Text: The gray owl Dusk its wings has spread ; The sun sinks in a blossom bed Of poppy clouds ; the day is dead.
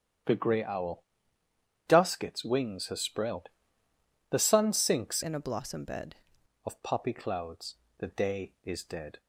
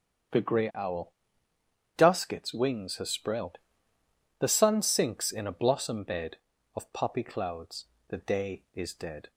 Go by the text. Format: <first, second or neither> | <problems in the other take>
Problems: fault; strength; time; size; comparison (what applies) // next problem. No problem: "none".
second | starts louder than the rest; strong; until 2.1 s; 9.5 dB; strong in the second // pauses between "owl" and "Dusk"; noticeable; at 1.0 s; 0.84 s long; noticeable in the second // changes voice from "in" to "bed"; from 5.2 to 6.1 s; 0.9 s long